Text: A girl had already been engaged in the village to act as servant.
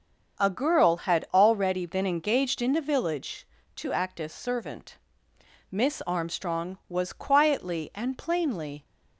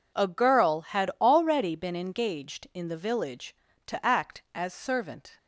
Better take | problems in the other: second | starts louder than the rest; until 1.4 s; 7 dB // goes on to say "Miss Armstrong was quietly and plainly"; strong; from 5.7 s on; 3.1 s long

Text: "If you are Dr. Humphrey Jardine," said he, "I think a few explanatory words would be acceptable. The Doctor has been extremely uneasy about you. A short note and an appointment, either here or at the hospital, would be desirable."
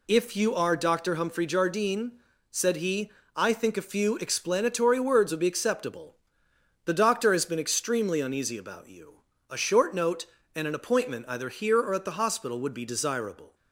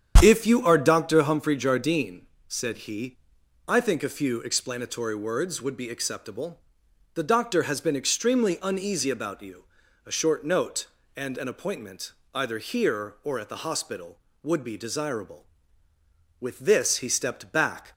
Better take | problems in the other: first | starts louder than the rest; strong; until 1.2 s; 8.5 dB // goes on to say "With this he stepped back"; from 16.4 s on; 1.5 s long

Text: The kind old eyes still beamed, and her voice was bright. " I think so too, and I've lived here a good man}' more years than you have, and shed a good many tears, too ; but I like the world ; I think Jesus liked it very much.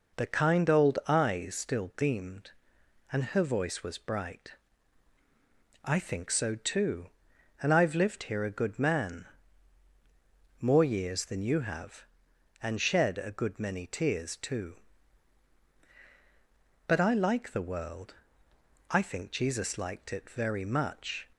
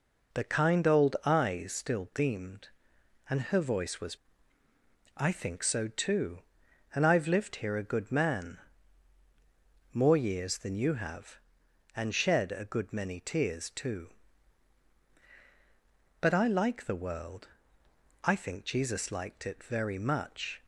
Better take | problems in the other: first | skips "bright"; at 4.3 s

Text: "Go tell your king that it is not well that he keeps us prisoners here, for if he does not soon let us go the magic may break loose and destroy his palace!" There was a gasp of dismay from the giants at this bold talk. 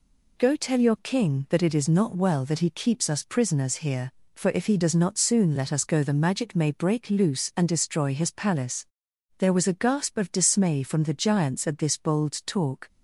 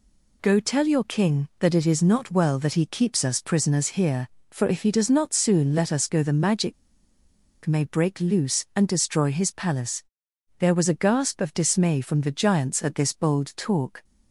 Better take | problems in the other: first | pauses between "magic" and "may"; noticeable; at 6.7 s; 0.90 s long

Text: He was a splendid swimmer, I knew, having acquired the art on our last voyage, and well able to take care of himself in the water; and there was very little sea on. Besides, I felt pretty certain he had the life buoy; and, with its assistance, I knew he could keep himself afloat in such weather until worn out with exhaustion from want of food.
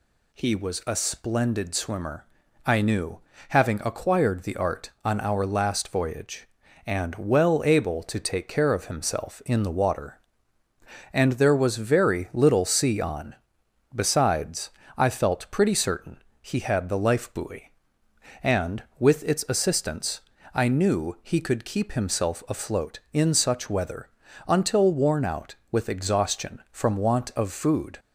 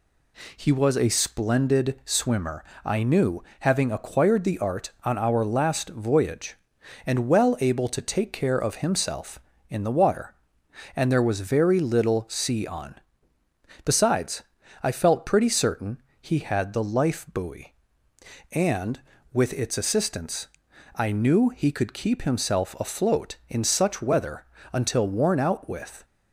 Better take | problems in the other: first | pauses between "certain" and "he"; slight; at 16.0 s; 0.18 s long; slight in the first // pauses between "weather" and "until"; slight; at 24.4 s; 0.34 s long; also in the first // stops before "exhaustion from want of food"; at 26.0 s

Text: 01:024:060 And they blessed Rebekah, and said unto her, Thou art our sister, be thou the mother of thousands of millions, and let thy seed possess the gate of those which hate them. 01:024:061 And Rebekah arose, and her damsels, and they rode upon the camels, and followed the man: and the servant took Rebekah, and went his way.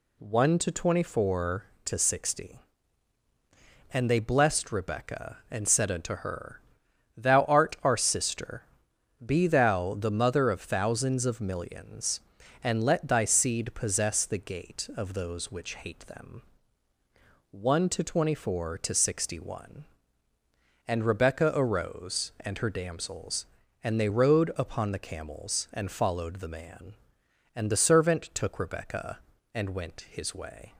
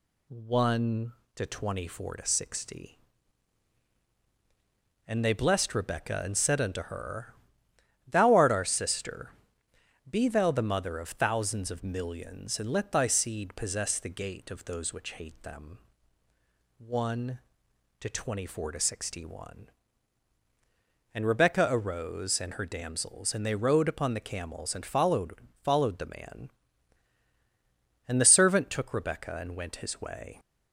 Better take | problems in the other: first | says "followed" twice; at 25.6 s

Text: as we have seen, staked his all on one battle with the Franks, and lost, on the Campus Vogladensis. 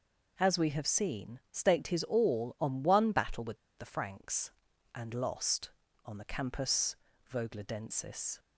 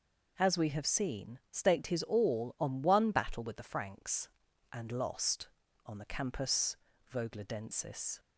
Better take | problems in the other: second | pauses between "with" and "the"; slight; at 3.5 s; 0.21 s long // pauses between "Campus" and "Vogladensis"; slight; at 6.9 s; 0.36 s long; slight in the second

